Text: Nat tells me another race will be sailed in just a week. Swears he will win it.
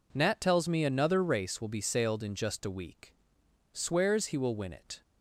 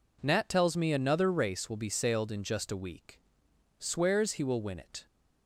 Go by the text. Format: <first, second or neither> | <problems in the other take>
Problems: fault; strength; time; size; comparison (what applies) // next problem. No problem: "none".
neither | none